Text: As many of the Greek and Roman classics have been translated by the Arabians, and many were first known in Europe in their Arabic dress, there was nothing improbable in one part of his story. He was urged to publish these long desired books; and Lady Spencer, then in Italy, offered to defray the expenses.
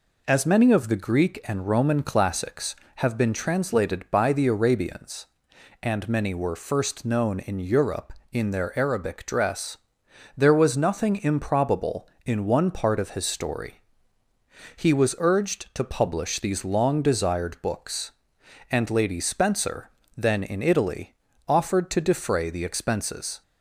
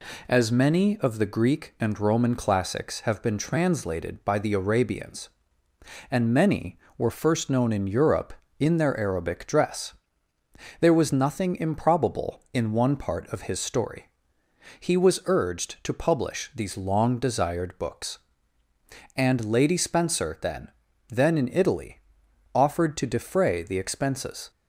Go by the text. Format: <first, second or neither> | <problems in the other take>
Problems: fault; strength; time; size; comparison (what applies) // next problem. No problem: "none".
first | says "then" twice; at 21.0 s